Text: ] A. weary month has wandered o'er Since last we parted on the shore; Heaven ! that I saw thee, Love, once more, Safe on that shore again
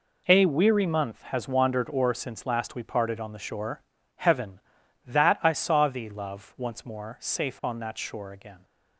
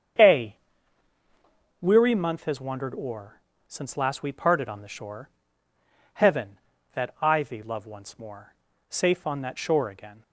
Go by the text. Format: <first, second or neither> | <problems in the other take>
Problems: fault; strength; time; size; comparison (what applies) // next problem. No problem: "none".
first | starts louder than the rest; strong; until 2.4 s; 7.5 dB // pauses between "o'er" and "Since"; slight; at 3.3 s; 0.28 s long // skips "saw"; at 7.4 s